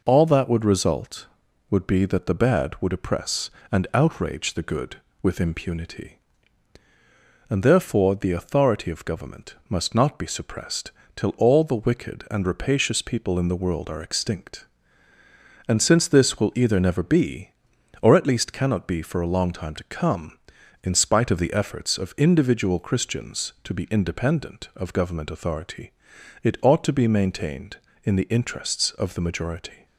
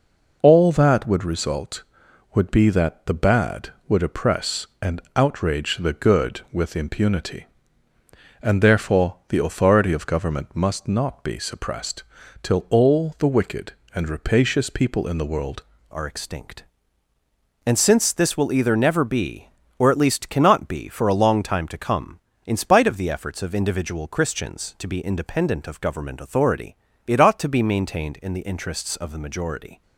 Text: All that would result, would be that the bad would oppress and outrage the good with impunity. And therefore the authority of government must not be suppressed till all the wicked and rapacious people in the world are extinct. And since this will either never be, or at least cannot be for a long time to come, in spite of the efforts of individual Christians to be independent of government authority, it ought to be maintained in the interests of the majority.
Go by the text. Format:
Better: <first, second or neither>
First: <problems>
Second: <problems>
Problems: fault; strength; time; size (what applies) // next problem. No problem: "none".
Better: first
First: pauses between "suppressed" and "till"; slight; at 10.9 s; 0.24 s long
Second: pauses between "suppressed" and "till"; at 12.0 s; 0.40 s long // changes voice at "are"; from 15.9 s on; 13.9 s long